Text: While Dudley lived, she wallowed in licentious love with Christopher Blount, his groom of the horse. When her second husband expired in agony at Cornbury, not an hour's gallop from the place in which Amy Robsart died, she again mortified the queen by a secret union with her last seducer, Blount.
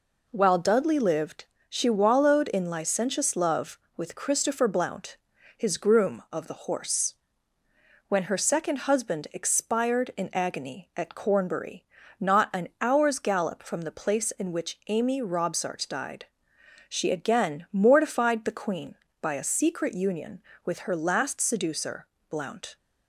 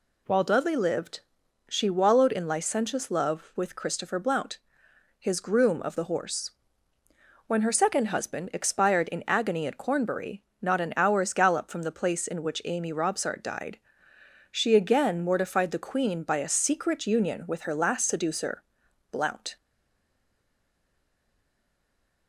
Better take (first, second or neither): first